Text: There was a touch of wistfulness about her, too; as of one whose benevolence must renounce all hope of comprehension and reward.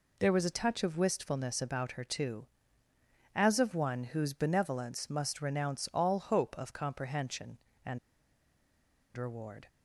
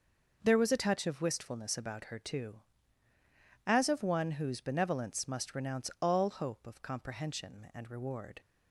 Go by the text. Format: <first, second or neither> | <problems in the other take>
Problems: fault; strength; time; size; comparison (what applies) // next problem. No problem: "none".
second | pauses between "and" and "reward"; at 7.9 s; 1.1 s long